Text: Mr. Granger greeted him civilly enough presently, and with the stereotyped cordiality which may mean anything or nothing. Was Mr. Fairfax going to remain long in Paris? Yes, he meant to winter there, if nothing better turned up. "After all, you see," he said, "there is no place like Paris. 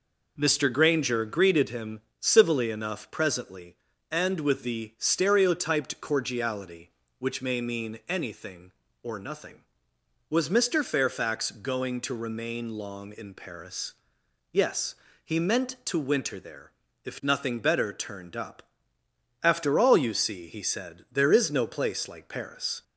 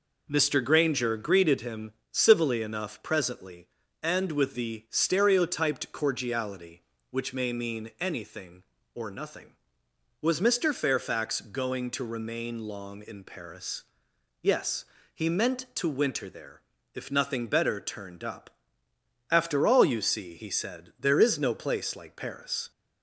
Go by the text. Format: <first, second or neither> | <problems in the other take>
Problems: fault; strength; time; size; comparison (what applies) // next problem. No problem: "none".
neither | pauses between "him" and "civilly"; slight; the same in both